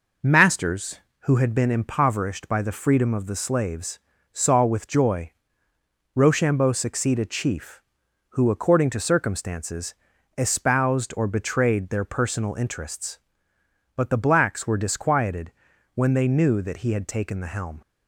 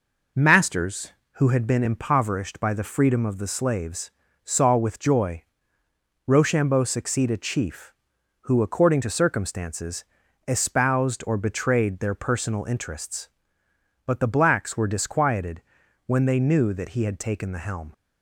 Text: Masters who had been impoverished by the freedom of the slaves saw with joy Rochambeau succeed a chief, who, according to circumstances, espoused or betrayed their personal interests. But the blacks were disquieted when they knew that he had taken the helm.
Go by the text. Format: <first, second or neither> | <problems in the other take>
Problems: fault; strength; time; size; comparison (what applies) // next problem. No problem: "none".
neither | pauses between "slaves" and "saw"; slight; the same in both // pauses between "joy" and "Rochambeau"; noticeable; the same in both // pauses between "disquieted" and "when"; the same in both